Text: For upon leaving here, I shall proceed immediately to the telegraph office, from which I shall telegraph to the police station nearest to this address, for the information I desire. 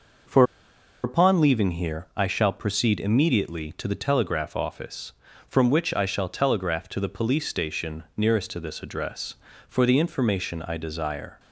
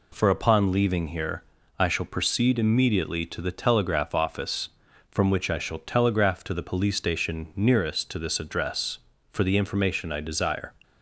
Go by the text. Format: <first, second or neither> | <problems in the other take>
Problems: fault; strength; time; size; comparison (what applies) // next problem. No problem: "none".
second | pauses between "For" and "upon"; noticeable; at 0.4 s; 0.60 s long